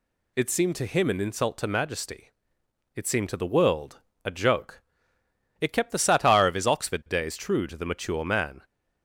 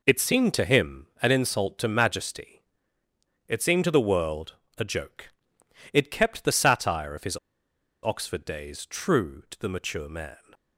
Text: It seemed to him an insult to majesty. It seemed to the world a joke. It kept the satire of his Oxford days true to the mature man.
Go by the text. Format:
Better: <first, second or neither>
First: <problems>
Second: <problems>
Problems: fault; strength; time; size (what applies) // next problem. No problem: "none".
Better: first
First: pauses between "world" and "a"; slight; at 3.9 s; 0.26 s long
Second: pauses between "world" and "a"; slight; at 4.5 s; 0.22 s long // pauses between "his" and "Oxford"; noticeable; at 7.3 s; 0.66 s long